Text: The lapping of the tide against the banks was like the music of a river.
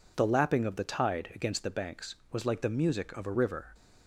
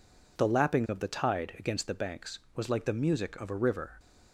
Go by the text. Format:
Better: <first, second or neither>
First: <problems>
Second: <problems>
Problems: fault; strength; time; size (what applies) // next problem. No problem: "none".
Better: neither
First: none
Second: none